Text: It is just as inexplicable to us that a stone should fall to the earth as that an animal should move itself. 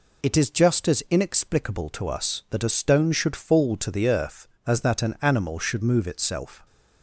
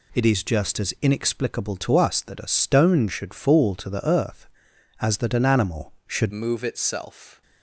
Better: first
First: none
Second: changes voice at "move"; from 6.3 s on; 1.1 s long

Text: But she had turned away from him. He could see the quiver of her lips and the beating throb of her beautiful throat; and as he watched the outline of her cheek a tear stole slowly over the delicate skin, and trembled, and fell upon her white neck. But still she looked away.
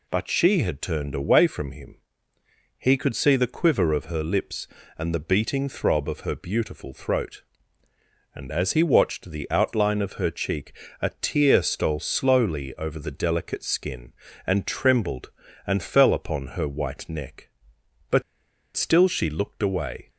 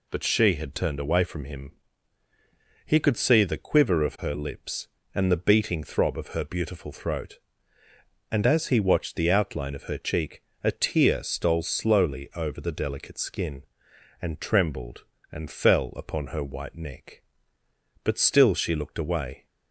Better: second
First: pauses between "cheek" and "a"; slight; at 10.7 s; 0.30 s long // pauses between "But" and "still"; noticeable; at 18.2 s; 0.52 s long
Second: pauses between "cheek" and "a"; slight; at 10.4 s; 0.22 s long

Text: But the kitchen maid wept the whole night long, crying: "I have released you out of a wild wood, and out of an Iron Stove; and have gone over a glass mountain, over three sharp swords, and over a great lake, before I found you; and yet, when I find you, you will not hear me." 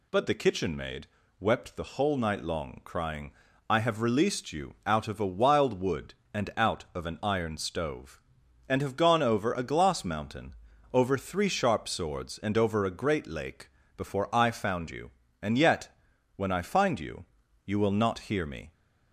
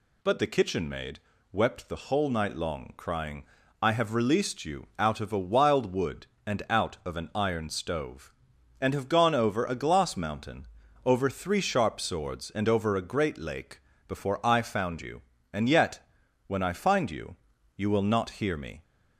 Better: neither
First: pauses between "maid" and "wept"; slight; at 1.0 s; 0.32 s long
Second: pauses between "maid" and "wept"; slight; at 1.1 s; 0.32 s long

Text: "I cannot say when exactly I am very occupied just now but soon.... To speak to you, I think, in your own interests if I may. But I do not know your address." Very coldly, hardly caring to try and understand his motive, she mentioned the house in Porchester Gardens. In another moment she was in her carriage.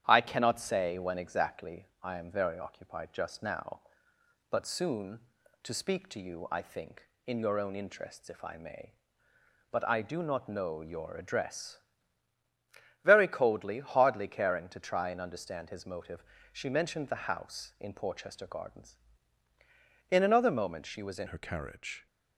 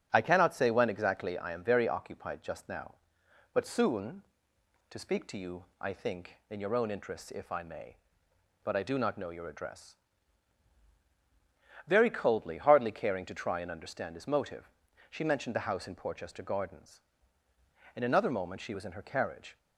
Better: second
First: starts louder than the rest; strong; until 1.0 s; 10 dB // pauses between "exactly" and "I"; slight; at 1.8 s; 0.16 s long // changes voice at "her"; from 21.2 s on; 0.8 s long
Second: starts louder than the rest; strong; until 1.1 s; 8.5 dB

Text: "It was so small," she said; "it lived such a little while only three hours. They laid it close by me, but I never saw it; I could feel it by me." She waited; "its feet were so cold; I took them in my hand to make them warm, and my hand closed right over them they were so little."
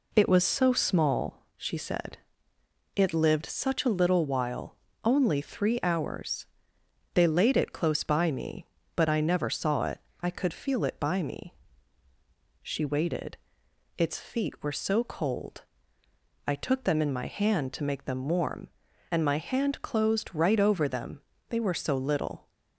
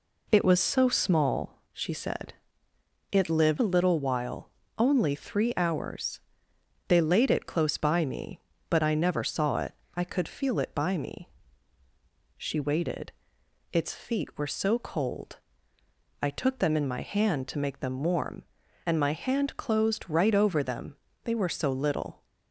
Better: first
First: pauses between "while" and "only"; slight; at 4.7 s; 0.30 s long // pauses between "them" and "they"; slight; at 21.2 s; 0.30 s long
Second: skips "such"; at 3.5 s // pauses between "while" and "only"; slight; at 4.4 s; 0.30 s long // pauses between "them" and "they"; slight; at 20.9 s; 0.30 s long

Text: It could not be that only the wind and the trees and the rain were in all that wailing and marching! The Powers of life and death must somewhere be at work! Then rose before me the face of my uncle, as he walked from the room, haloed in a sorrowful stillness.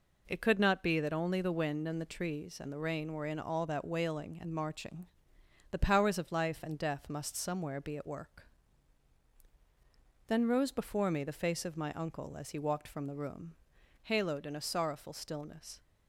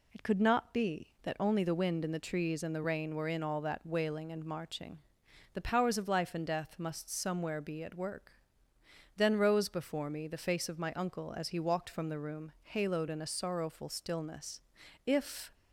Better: first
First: none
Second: goes on to say "If"; slight; from 15.0 s on; 0.48 s long

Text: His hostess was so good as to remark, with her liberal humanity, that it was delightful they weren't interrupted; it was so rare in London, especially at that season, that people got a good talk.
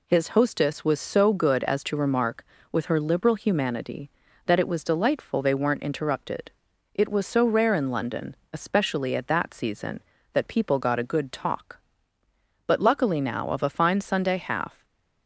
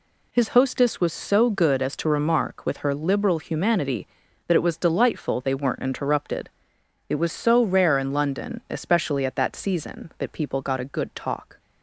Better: second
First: goes on to say "But luckily now of a fine Sunday half"; strong; from 12.6 s on; 2.1 s long // stays silent after the last word; slight; from 14.7 s on; 0.5 s long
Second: none

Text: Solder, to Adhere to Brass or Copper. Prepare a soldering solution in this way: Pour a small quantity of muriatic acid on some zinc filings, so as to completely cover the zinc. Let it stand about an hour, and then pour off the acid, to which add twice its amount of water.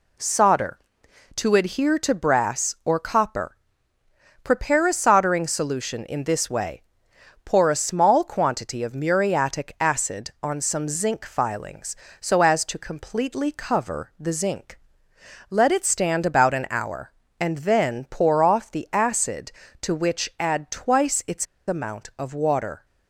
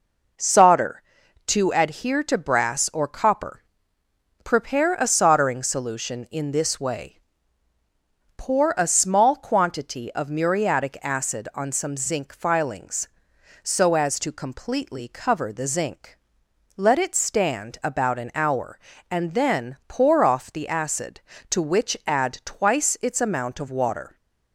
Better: second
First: pauses between "its" and "amount"; slight; at 21.4 s; 0.22 s long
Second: none

